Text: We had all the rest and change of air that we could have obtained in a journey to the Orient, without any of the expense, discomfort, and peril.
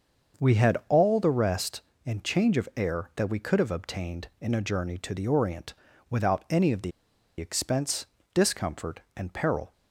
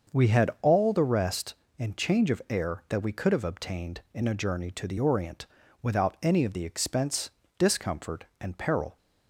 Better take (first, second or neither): second